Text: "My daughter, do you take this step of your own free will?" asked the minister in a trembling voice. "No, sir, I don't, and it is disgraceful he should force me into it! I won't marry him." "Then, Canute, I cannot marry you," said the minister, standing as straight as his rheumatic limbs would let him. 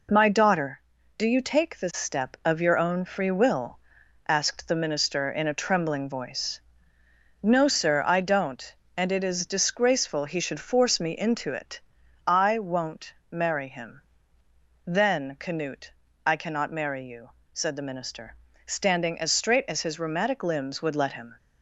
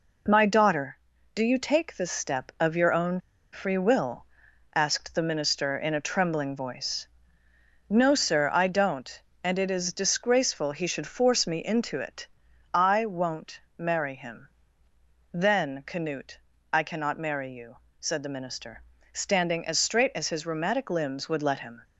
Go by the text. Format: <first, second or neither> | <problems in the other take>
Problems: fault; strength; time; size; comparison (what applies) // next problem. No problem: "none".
first | pauses between "own" and "free"; slight; at 3.2 s; 0.31 s long // pauses between "won't" and "marry"; slight; at 13.6 s; 0.16 s long; slight in the first